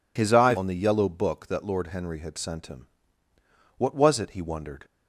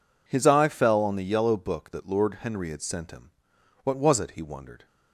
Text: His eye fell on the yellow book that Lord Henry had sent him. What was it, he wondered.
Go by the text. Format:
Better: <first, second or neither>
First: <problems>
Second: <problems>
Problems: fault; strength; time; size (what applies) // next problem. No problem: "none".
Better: second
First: skips "fell"; at 0.5 s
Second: none